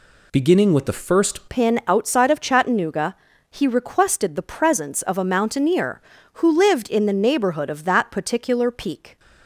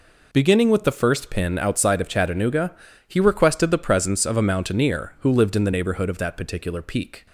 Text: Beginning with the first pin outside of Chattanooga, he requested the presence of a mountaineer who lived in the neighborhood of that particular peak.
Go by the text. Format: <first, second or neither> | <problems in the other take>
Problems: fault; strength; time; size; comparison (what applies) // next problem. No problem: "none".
second | changes voice at "pin"; from 1.4 s on; 7.7 s long